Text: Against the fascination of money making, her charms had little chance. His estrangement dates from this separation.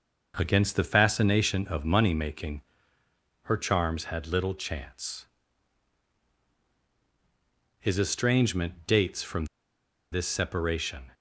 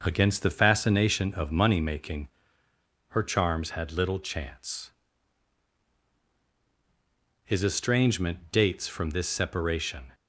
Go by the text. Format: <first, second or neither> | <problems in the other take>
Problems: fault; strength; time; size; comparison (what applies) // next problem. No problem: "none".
second | starts louder than the rest; noticeable; until 1.3 s; 6 dB; noticeable in the second // pauses between "from" and "this"; noticeable; at 9.4 s; 0.66 s long